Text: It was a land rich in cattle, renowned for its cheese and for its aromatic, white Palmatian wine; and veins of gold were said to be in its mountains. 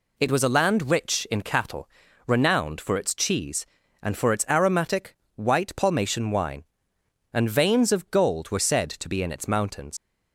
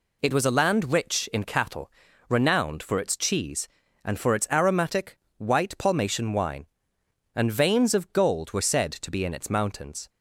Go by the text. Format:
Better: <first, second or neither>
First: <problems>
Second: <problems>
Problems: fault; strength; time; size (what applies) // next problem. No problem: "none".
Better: second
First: leaves "mountains" unfinished; at 9.9 s; 100 ms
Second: none